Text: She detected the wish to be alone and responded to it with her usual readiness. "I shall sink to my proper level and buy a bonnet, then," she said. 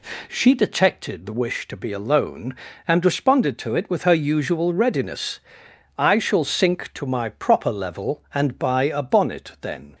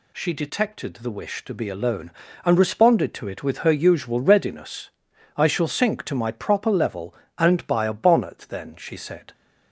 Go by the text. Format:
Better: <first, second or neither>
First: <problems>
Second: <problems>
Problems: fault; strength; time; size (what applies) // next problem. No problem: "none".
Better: second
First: stops before "she said"; at 9.9 s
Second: none